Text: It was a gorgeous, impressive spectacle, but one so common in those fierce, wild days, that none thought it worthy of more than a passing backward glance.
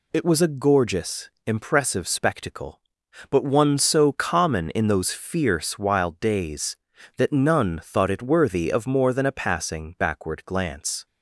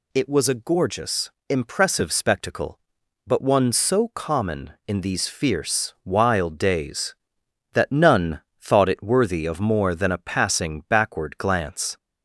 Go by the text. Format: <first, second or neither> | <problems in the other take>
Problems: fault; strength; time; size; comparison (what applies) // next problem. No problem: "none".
first | says "these" for "those"; at 5.0 s // pauses between "none" and "thought"; slight; at 8.4 s; 0.20 s long